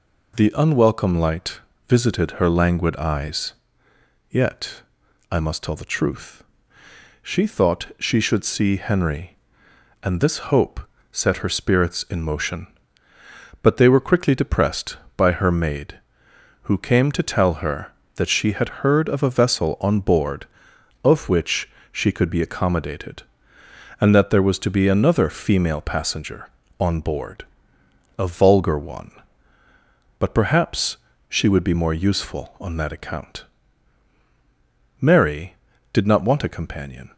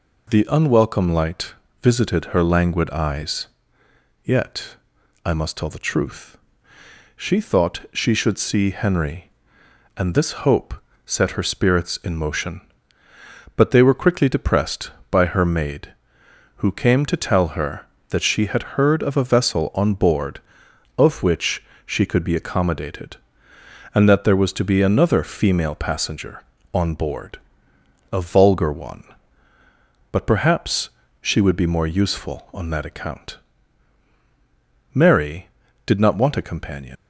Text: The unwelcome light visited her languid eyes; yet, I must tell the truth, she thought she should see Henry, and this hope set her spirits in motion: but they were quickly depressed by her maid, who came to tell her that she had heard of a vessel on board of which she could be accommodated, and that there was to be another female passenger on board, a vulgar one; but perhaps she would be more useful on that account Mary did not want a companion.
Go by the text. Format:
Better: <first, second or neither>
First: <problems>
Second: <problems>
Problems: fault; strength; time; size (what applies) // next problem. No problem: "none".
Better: first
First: pauses between "light" and "visited"; slight; at 1.6 s; 0.28 s long // pauses between "hope" and "set"; slight; at 10.8 s; 0.32 s long // pauses between "which" and "she"; slight; at 21.7 s; 0.22 s long // pauses between "perhaps" and "she"; slight; at 30.9 s; 0.32 s long // pauses between "account" and "Mary"; strong; at 33.4 s; 1.5 s long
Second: pauses between "light" and "visited"; slight; at 1.5 s; 0.28 s long // pauses between "hope" and "set"; slight; at 10.7 s; 0.32 s long // pauses between "which" and "she"; slight; at 21.6 s; 0.22 s long // pauses between "perhaps" and "she"; slight; at 30.8 s; 0.32 s long // pauses between "account" and "Mary"; strong; at 33.3 s; 1.5 s long // leaves "companion" unfinished; at 36.9 s; 115 ms